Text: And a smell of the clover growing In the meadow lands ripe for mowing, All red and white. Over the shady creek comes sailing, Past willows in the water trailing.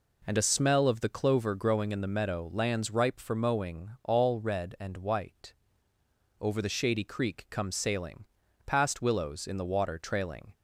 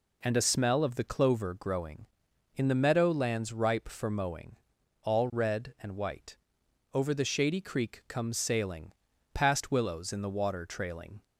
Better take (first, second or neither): neither